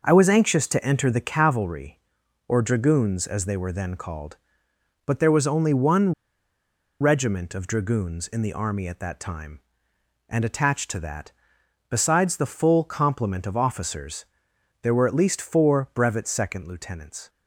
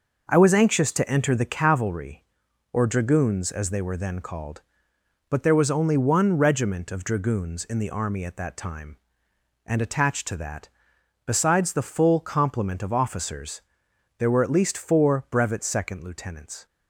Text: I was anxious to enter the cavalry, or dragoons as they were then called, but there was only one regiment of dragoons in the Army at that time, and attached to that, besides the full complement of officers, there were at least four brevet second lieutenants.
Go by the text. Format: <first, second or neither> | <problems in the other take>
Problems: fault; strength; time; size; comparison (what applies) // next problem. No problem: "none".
second | pauses between "one" and "regiment"; noticeable; at 6.1 s; 0.88 s long